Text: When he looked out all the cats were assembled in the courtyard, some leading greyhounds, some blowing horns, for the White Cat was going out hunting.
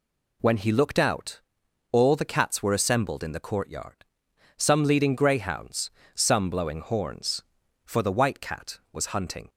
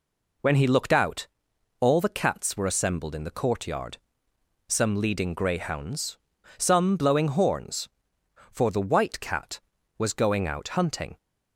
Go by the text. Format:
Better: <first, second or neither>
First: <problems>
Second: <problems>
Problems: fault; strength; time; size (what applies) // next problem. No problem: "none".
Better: second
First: pauses between "out" and "all"; noticeable; at 1.4 s; 0.52 s long // skips "going out"; at 9.0 s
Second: pauses between "out" and "all"; noticeable; at 1.2 s; 0.54 s long